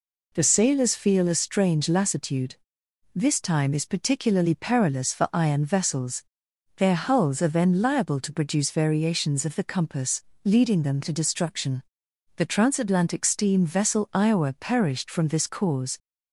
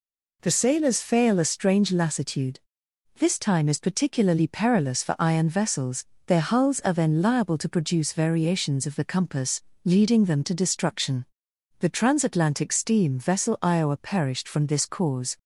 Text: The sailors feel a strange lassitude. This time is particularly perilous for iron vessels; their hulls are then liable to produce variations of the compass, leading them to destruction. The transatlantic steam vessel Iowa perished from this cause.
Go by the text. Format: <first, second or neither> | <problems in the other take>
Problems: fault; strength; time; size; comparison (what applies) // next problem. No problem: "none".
first | says "fail" for "feel"; at 1.0 s